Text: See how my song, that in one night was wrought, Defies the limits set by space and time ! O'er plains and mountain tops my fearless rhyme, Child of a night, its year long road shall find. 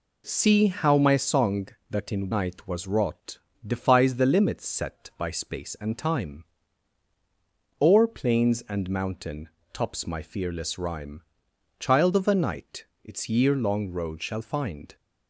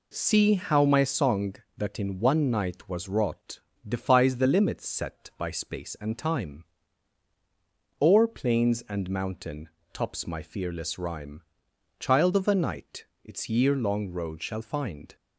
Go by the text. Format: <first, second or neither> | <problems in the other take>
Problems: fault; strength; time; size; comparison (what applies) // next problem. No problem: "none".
second | skips "one"; at 2.3 s // pauses between "mountain" and "tops"; slight; at 9.4 s; 0.24 s long; slight in the second